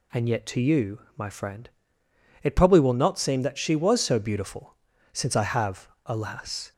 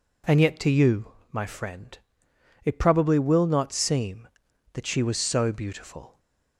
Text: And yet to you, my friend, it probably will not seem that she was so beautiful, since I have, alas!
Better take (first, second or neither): first